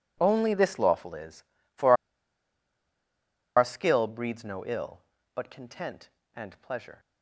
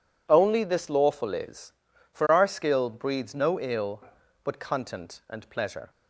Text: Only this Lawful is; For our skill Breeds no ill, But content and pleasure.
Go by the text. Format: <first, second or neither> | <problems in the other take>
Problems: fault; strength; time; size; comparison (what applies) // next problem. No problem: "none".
second | pauses between "For" and "our"; strong; at 1.9 s; 1.6 s long